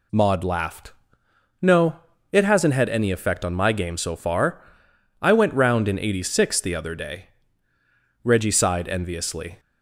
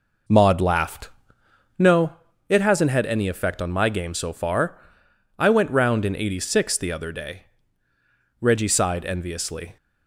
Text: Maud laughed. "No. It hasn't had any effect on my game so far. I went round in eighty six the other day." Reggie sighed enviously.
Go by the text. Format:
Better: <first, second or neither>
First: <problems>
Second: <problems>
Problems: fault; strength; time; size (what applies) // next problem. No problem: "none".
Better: first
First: none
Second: starts louder than the rest; noticeable; until 1.9 s; 5 dB